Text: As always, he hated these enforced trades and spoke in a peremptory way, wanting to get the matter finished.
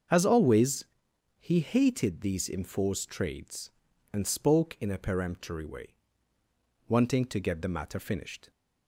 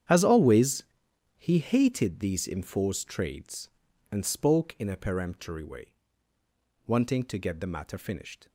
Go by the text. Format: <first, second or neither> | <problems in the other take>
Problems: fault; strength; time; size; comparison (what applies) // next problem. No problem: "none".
first | gets quieter; strong; throughout; 15 dB // starts louder than the rest; strong; until 1.6 s; 9 dB; also in the first